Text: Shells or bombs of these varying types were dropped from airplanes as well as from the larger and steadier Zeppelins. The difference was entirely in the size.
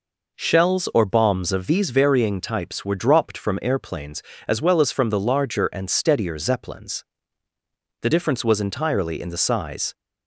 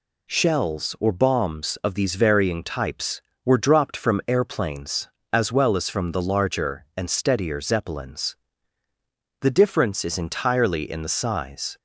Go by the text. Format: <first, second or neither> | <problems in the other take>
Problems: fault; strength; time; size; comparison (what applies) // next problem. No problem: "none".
first | says "is" for "was"; at 10.0 s